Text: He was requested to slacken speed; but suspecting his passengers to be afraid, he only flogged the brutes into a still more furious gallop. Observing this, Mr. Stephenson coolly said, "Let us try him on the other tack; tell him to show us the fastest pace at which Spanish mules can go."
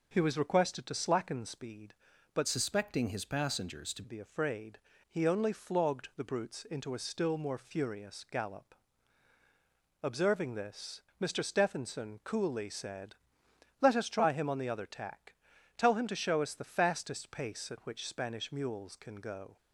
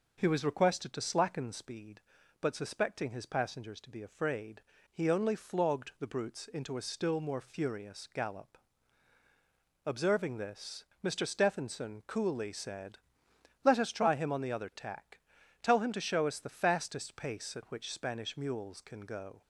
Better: second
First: changes voice from "suspecting" to "to"; from 2.4 to 4.0 s; 1.6 s long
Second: none

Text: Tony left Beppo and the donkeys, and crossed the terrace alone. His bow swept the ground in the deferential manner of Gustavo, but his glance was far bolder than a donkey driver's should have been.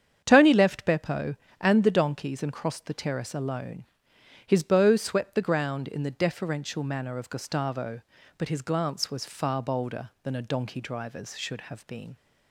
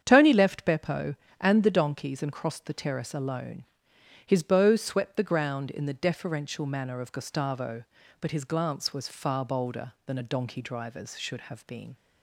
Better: neither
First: starts louder than the rest; strong; until 1.2 s; 8 dB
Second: starts louder than the rest; strong; until 1.0 s; 8.5 dB

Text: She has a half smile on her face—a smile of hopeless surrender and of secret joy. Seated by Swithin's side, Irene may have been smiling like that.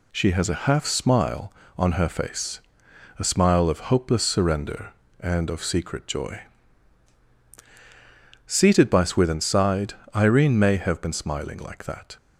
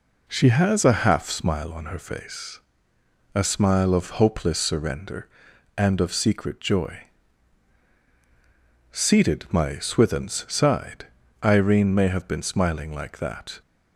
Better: first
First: none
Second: says "my" for "by"; at 9.5 s

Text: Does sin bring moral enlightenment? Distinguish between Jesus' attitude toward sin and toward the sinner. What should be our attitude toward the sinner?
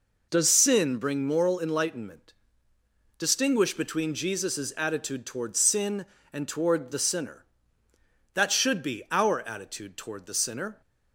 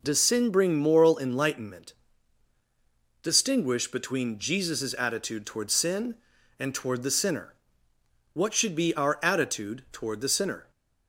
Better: second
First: says "That" for "What"; at 8.3 s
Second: none

